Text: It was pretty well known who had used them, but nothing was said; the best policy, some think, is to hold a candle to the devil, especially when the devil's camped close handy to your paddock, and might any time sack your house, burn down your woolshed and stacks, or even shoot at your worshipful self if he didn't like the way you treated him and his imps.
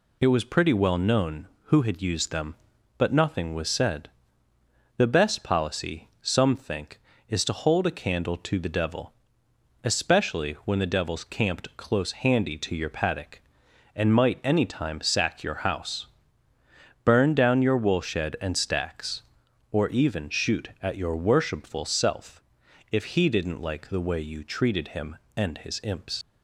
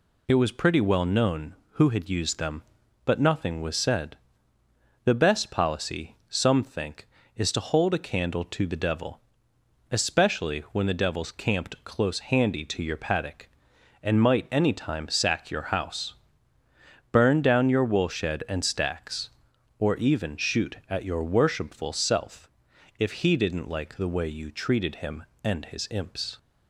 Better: second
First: pauses between "self" and "if"; noticeable; at 22.4 s; 0.52 s long // leaves "imps" unfinished; at 26.2 s; 90 ms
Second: pauses between "self" and "if"; noticeable; at 22.4 s; 0.52 s long

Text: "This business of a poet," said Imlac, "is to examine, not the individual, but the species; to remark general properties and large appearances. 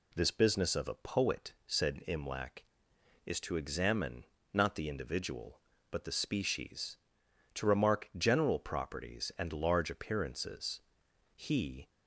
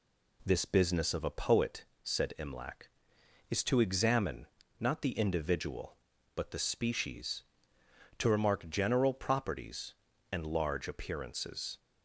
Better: second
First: goes on to say "He"; from 11.3 s on; 0.56 s long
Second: none

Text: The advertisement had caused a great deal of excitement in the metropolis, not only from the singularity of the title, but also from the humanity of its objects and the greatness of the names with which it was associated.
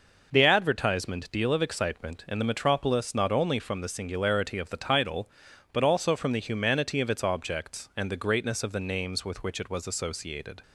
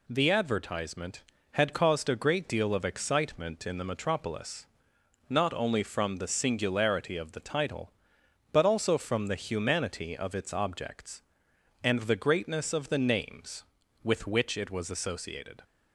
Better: second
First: skips "had caused a great"; at 1.2 s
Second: none

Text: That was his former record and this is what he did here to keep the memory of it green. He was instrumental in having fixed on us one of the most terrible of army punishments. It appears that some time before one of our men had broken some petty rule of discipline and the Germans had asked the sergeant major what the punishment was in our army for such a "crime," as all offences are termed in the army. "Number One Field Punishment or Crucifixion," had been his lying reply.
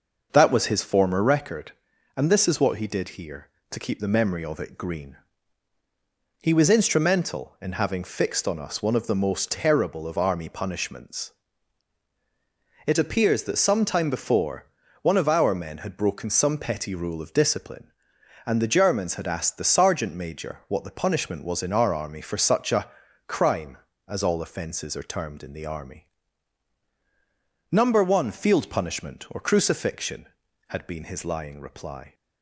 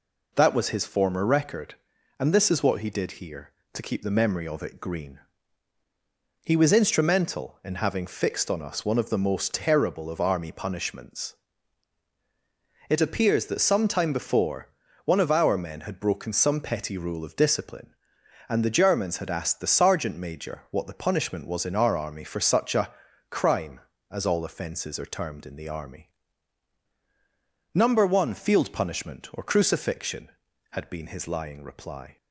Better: second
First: starts louder than the rest; noticeable; until 1.4 s; 6 dB // pauses between "before" and "one"; slight; at 14.6 s; 0.36 s long // pauses between "a" and "crime"; at 22.8 s; 0.40 s long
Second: pauses between "before" and "one"; slight; at 14.6 s; 0.36 s long // pauses between "a" and "crime"; at 22.9 s; 0.40 s long

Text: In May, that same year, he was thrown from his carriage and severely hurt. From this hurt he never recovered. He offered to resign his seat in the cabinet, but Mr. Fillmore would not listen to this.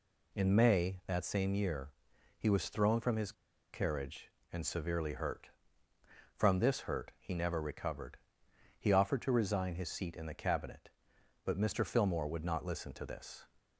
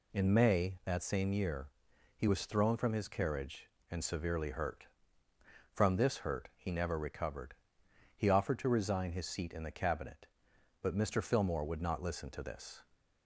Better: second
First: pauses between "his" and "carriage"; at 3.3 s; 0.41 s long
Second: none

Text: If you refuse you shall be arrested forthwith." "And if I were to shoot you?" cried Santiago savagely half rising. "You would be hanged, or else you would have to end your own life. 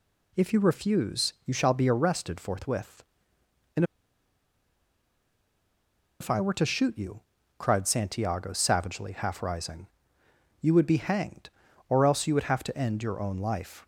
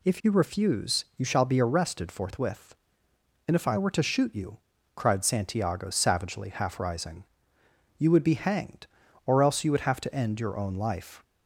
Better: second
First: pauses between "And" and "if"; strong; at 3.8 s; 2.3 s long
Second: none

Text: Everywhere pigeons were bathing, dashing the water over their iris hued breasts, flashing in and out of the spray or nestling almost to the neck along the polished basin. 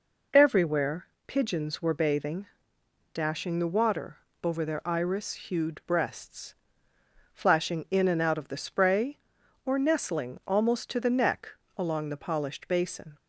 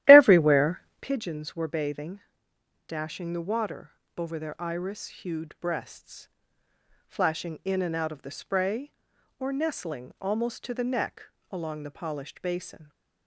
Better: first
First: pauses between "Everywhere" and "pigeons"; slight; at 1.0 s; 0.18 s long // pauses between "water" and "over"; slight; at 4.1 s; 0.26 s long // pauses between "neck" and "along"; slight; at 11.4 s; 0.28 s long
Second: starts louder than the rest; strong; until 1.1 s; 13.5 dB // pauses between "Everywhere" and "pigeons"; slight; at 0.8 s; 0.18 s long // pauses between "water" and "over"; slight; at 3.9 s; 0.26 s long // pauses between "neck" and "along"; slight; at 11.2 s; 0.28 s long

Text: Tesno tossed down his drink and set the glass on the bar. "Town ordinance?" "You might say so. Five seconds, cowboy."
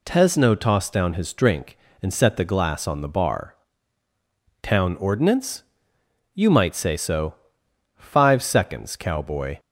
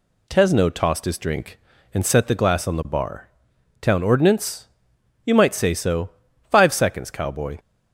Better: first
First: none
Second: skips "down"; at 1.0 s

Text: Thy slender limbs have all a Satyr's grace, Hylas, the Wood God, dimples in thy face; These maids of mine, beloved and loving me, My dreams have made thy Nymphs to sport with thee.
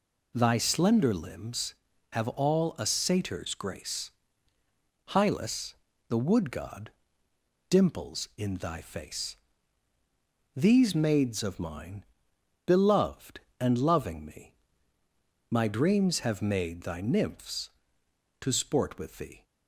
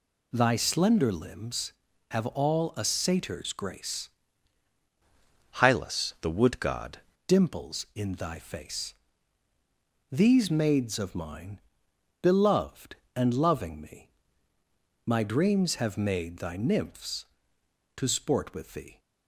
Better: first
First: none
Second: changes voice from "Hylas" to "God"; from 5.5 to 6.9 s; 1.4 s long

